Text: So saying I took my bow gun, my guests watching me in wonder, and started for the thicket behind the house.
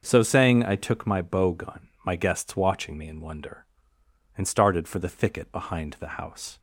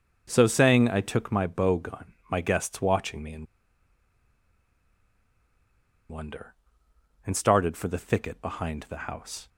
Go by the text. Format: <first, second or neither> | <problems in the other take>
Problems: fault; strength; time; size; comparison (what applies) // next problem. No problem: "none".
first | starts louder than the rest; until 1.2 s; 6 dB; noticeable in the first // pauses between "in" and "wonder"; strong; at 3.4 s; 2.6 s long